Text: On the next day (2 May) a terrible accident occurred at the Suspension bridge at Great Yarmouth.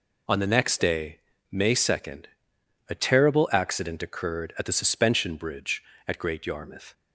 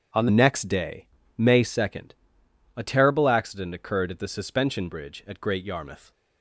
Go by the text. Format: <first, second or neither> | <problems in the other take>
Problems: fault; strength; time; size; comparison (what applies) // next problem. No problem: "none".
first | starts louder than the rest; strong; until 1.4 s; 8 dB // changes voice at "next"; from 0.2 s on; 5.9 s long